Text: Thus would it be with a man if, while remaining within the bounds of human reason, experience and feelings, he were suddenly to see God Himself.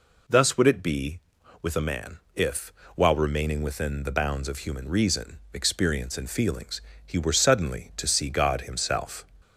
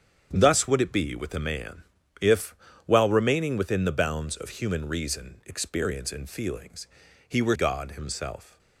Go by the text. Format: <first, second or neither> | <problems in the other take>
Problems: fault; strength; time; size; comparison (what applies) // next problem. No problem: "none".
first | starts louder than the rest; strong; until 1.3 s; 8 dB // pauses between "man" and "if"; at 1.8 s; 0.38 s long; slight in the first // skips "suddenly to see"; at 7.5 s